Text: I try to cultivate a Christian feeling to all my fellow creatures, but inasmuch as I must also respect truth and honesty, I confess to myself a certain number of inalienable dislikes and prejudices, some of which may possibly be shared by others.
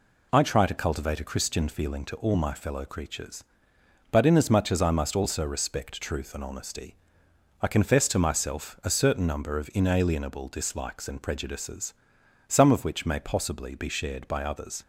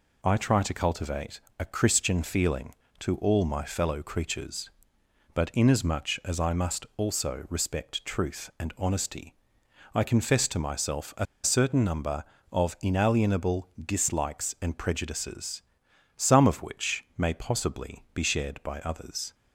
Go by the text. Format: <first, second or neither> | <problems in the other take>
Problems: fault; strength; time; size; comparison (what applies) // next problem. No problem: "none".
first | pauses between "cultivate" and "a"; slight; at 1.3 s; 0.18 s long // pauses between "a" and "certain"; slight; at 11.2 s; 0.18 s long // pauses between "inalienable" and "dislikes"; slight; at 13.6 s; 0.16 s long